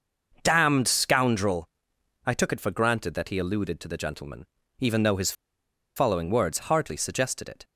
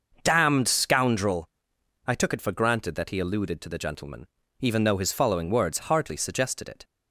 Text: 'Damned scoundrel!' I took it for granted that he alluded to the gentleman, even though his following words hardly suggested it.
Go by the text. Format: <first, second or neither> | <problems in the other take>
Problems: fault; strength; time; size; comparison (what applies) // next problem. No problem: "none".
second | pauses between "his" and "following"; noticeable; at 5.3 s; 0.63 s long